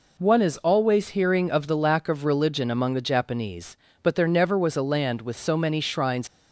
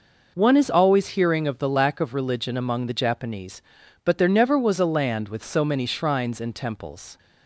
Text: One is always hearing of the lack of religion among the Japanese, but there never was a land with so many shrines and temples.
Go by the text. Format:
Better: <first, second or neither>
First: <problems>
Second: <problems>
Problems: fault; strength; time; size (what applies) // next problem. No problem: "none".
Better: second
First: stops before "and temples"; at 6.2 s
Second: none